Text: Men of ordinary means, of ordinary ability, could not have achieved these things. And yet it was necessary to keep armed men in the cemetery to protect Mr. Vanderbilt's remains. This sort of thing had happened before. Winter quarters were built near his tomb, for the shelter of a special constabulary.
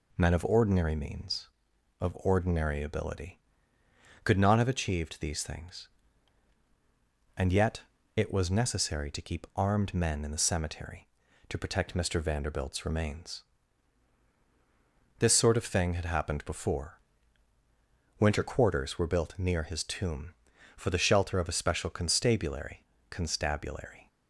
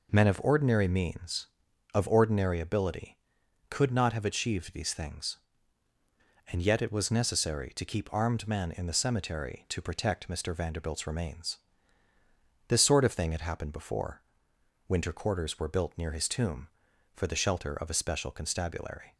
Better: second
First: pauses between "yet" and "it"; slight; at 7.8 s; 0.34 s long // says "constabulary" twice; at 23.0 s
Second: none

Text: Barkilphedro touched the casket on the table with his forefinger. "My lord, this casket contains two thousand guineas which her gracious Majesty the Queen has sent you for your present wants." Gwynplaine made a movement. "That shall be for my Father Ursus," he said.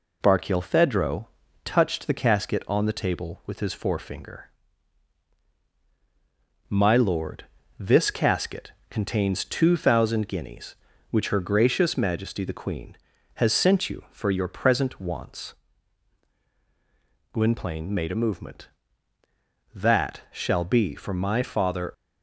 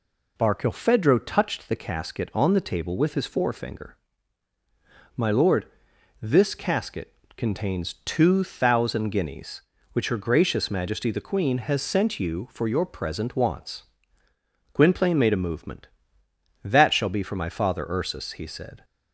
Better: second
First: pauses between "Barkilphedro" and "touched"; at 1.2 s; 0.38 s long // pauses between "casket" and "contains"; slight; at 8.7 s; 0.16 s long // stops before "Ursus he said"; at 21.9 s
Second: pauses between "casket" and "contains"; slight; at 7.1 s; 0.22 s long

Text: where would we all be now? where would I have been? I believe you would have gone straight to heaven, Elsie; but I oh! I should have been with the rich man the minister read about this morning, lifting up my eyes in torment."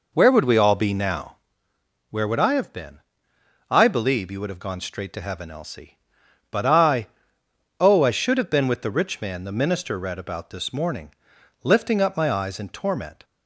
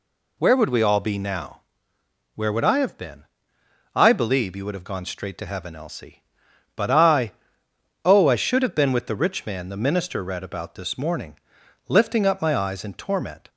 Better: second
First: starts louder than the rest; noticeable; until 1.6 s; 4.5 dB // pauses between "I" and "oh"; noticeable; at 7.0 s; 0.72 s long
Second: pauses between "I" and "oh"; noticeable; at 7.3 s; 0.72 s long

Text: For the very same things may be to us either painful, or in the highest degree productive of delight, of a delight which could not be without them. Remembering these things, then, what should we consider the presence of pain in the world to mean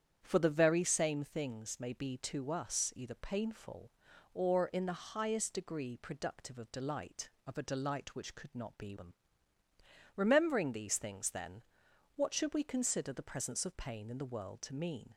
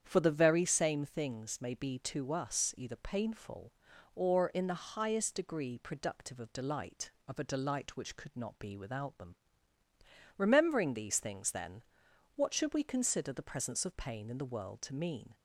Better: second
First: starts louder than the rest; strong; until 1.2 s; 8.5 dB // skips "without"; at 8.9 s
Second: starts louder than the rest; strong; until 1.0 s; 8.5 dB

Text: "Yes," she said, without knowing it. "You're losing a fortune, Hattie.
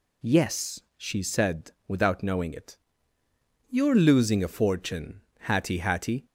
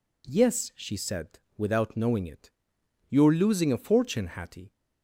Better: second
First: says "Hattie" twice; at 5.7 s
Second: none

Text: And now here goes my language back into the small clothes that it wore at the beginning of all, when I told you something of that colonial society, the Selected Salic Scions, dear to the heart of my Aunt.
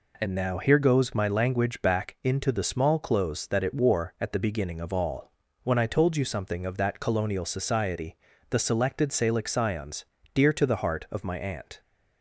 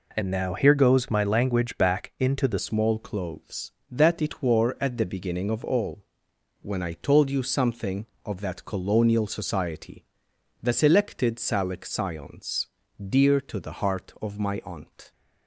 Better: first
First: none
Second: changes voice at "small"; from 2.5 s on; 12.6 s long

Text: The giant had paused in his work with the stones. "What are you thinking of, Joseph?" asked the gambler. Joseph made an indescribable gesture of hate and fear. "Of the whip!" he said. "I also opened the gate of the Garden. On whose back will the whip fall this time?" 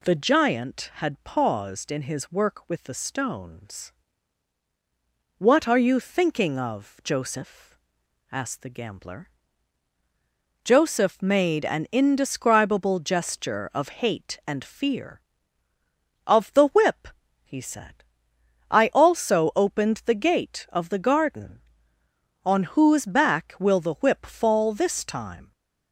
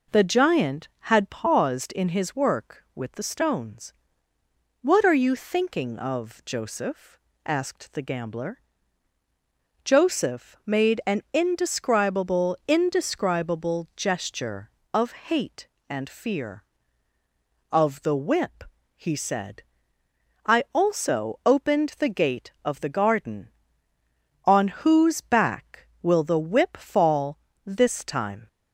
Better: first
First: none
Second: says "indescribable" twice; at 12.6 s // pauses between "of" and "hate"; slight; at 15.1 s; 0.16 s long // pauses between "fall" and "this"; slight; at 27.3 s; 0.28 s long

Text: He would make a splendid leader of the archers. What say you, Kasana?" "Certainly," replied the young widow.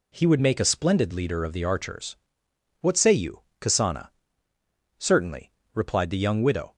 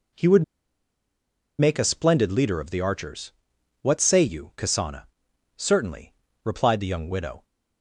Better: first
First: none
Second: pauses between "would" and "make"; at 0.4 s; 1.1 s long

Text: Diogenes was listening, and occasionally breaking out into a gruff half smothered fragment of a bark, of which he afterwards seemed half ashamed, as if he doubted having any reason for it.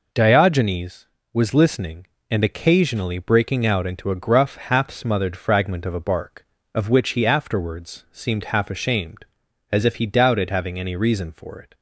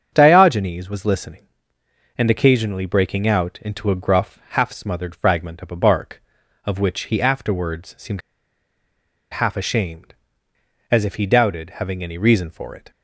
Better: first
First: none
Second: starts louder than the rest; strong; until 1.1 s; 8 dB // pauses between "seemed" and "half"; at 8.2 s; 1.1 s long

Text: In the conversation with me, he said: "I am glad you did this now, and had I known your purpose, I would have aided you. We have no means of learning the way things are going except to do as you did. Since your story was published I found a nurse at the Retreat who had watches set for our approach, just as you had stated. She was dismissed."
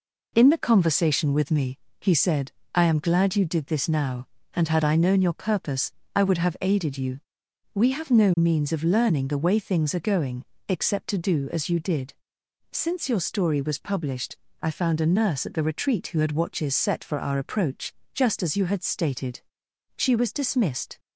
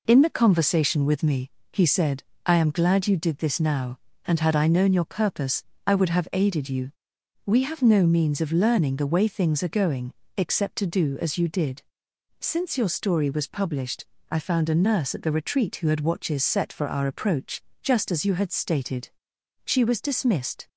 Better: neither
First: pauses between "going" and "except"; slight; at 10.4 s; 0.24 s long // pauses between "published" and "I"; slight; at 14.3 s; 0.24 s long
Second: pauses between "going" and "except"; slight; at 10.1 s; 0.24 s long // pauses between "published" and "I"; slight; at 14.0 s; 0.24 s long

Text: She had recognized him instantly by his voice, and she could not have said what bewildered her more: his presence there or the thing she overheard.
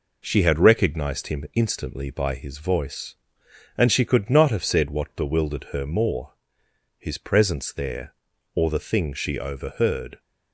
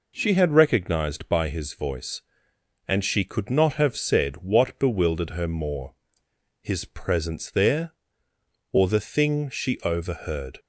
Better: first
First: none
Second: skips "him instantly"; at 1.2 s

